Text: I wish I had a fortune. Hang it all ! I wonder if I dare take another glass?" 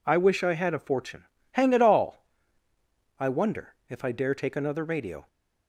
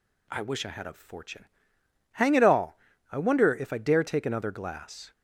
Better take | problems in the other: second | says "radio" for "glass"; at 4.8 s

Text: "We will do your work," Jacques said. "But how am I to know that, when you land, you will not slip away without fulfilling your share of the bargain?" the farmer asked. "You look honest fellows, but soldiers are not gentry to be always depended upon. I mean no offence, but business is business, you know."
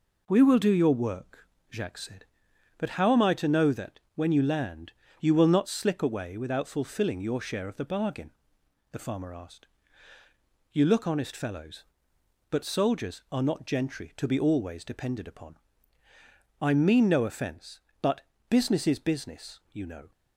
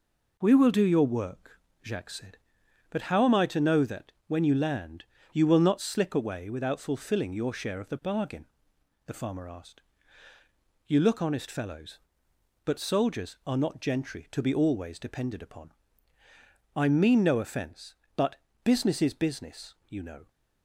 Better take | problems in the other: neither | pauses between "but" and "business"; slight; the same in both

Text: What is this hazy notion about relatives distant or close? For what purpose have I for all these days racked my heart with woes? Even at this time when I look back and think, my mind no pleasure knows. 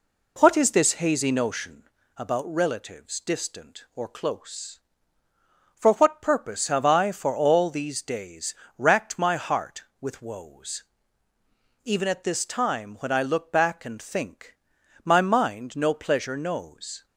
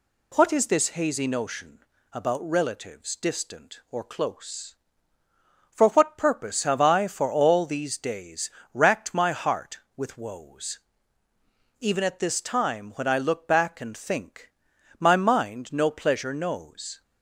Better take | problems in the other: second | starts louder than the rest; slight; until 1.9 s; 3 dB // pauses between "notion" and "about"; slight; at 1.8 s; 0.26 s long; slight in the second // pauses between "days" and "racked"; slight; at 8.5 s; 0.24 s long; slight in the second

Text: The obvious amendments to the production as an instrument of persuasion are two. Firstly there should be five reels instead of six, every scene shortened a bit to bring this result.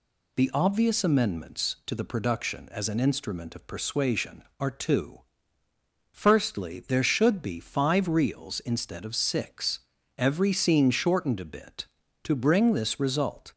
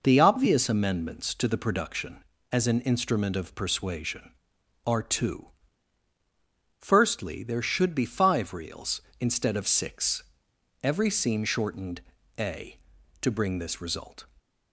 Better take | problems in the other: first | pauses between "shortened" and "a"; slight; at 12.0 s; 0.36 s long // skips "bit"; at 12.9 s

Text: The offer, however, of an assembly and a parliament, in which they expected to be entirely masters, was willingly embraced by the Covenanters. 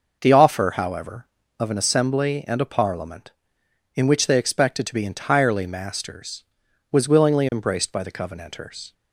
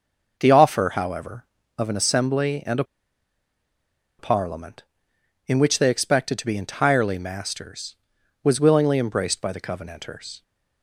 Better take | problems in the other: first | pauses between "a" and "parliament"; strong; at 2.8 s; 1.3 s long

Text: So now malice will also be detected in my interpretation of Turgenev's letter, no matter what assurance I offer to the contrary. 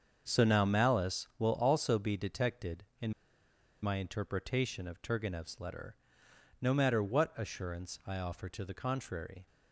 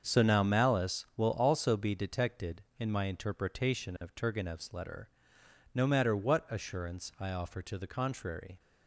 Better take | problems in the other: second | starts louder than the rest; until 1.2 s; 7 dB; also in the second // pauses between "in" and "my"; noticeable; at 3.1 s; 0.70 s long

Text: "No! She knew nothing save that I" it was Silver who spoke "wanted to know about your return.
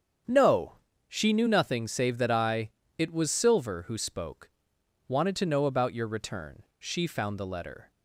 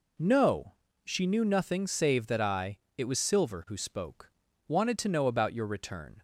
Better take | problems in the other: second | starts louder than the rest; strong; until 1.5 s; 7.5 dB // pauses between "I" and "it"; slight; at 2.6 s; 0.28 s long; slight in the second // pauses between "spoke" and "wanted"; noticeable; at 4.4 s; 0.56 s long; slight in the second // goes on to say "She found the letter"; noticeable; from 6.7 s on; 1.1 s long

